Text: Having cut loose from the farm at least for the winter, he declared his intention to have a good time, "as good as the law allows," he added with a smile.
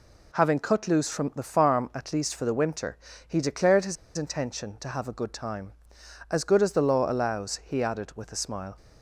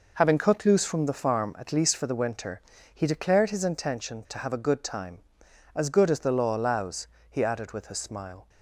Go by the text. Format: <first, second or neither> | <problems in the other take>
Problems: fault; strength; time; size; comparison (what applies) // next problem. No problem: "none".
second | pauses between "his" and "intention"; slight; at 3.9 s; 0.22 s long